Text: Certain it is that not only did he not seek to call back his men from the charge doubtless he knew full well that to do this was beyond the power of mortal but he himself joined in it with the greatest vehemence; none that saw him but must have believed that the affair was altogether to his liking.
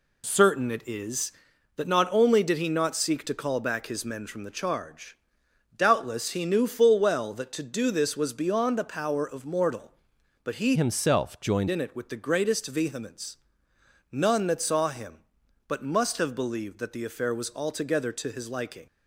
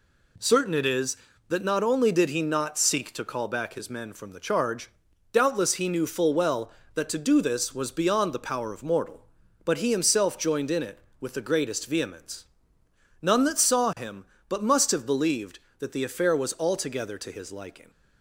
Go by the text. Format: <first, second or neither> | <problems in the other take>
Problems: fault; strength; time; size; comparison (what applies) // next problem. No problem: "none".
second | pauses between "charge" and "doubtless"; noticeable; at 5.1 s; 0.60 s long; also in the second // changes voice from "himself" to "joined"; from 10.7 to 11.6 s; 0.9 s long